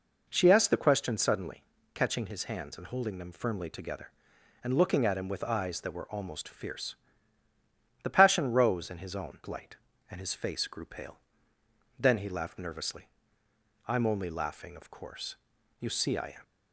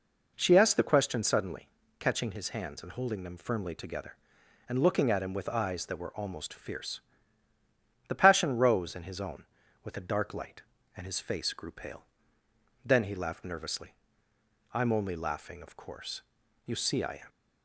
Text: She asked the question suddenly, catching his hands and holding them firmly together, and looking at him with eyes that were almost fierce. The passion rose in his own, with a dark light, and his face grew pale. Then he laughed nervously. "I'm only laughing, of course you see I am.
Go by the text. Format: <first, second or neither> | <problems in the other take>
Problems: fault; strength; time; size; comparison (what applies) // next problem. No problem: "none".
second | skips "with a dark"; at 9.4 s // pauses between "course" and "you"; at 15.3 s; 0.42 s long; also in the second